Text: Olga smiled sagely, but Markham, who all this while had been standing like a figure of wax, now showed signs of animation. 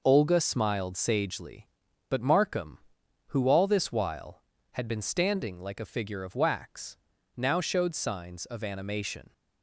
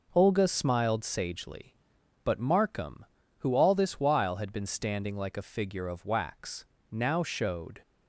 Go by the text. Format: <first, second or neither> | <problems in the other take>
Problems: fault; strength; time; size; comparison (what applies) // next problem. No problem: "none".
first | stops before "signs of animation"; at 7.8 s